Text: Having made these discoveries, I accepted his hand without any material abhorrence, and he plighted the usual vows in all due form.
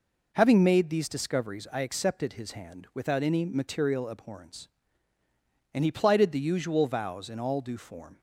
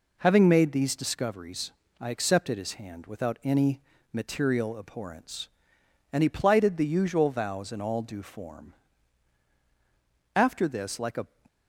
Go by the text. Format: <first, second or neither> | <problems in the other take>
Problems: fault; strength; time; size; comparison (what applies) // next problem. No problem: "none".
first | pauses between "any" and "material"; slight; at 3.7 s; 0.32 s long // goes on to say "After this like a"; noticeable; from 10.3 s on; 0.90 s long